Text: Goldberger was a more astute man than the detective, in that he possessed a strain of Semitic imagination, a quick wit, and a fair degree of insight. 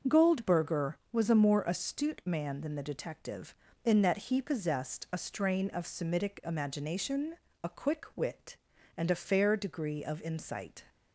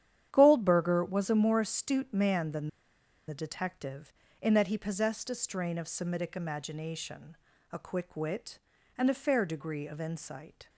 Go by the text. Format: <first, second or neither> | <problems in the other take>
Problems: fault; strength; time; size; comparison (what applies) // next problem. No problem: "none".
first | starts louder than the rest; strong; until 1.3 s; 10 dB // pauses between "than" and "the"; noticeable; at 2.6 s; 0.59 s long